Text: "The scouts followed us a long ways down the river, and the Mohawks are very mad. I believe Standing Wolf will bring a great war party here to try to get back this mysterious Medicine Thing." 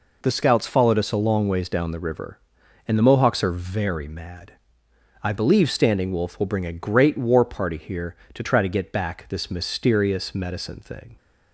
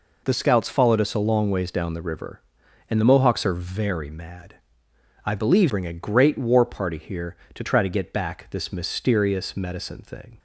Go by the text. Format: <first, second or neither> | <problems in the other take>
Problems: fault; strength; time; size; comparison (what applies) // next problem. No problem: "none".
first | skips "Standing Wolf will"; at 5.6 s